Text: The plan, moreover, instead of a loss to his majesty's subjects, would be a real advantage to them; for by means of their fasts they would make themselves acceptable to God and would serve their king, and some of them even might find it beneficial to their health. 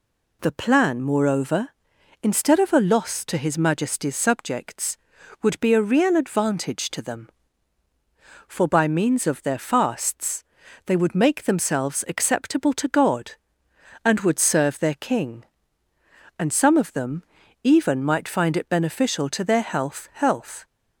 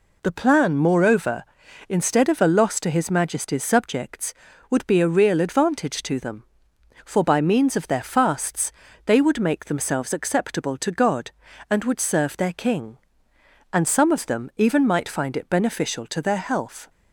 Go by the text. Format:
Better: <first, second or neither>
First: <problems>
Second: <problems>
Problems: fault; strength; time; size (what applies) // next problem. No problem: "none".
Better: second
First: pauses between "fasts" and "they"; at 10.4 s; 0.44 s long // pauses between "them" and "even"; at 17.2 s; 0.40 s long // says "health" twice; at 20.1 s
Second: pauses between "fasts" and "they"; slight; at 8.6 s; 0.36 s long